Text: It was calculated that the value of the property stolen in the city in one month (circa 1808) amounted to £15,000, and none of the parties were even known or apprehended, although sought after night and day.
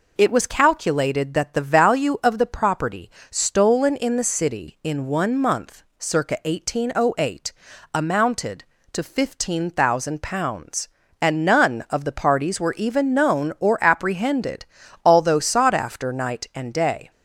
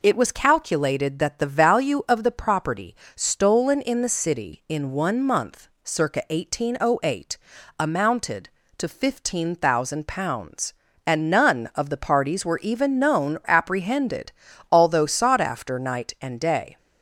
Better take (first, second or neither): first